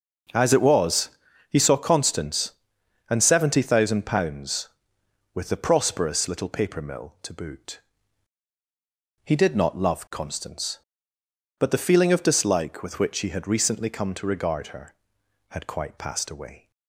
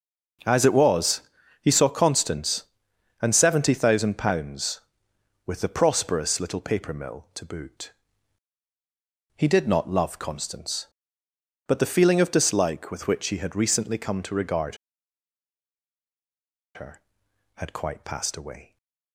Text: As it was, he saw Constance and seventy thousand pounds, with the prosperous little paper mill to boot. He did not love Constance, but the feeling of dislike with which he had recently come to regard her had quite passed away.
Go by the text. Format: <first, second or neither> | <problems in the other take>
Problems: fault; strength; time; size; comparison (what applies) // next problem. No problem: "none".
first | starts louder than the rest; noticeable; until 1.8 s; 6 dB; noticeable in the first // pauses between "regard" and "her"; strong; at 14.7 s; 1.9 s long